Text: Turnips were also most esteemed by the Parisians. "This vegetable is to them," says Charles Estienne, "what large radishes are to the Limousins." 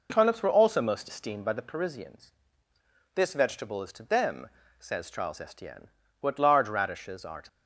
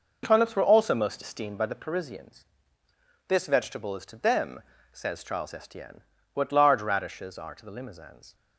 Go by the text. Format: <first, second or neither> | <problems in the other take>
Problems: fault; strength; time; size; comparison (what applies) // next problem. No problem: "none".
second | stops before "the Limousins"; at 7.4 s